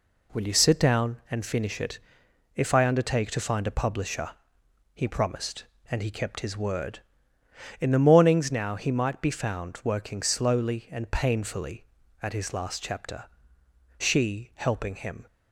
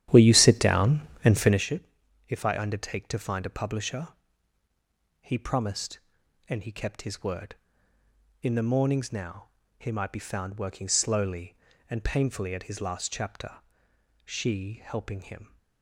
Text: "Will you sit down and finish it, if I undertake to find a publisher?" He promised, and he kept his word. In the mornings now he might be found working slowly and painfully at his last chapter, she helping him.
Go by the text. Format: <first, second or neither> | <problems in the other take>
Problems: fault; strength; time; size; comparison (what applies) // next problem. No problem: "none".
first | starts louder than the rest; strong; until 1.6 s; 11.5 dB // pauses between "now" and "he"; slight; at 9.4 s; 0.28 s long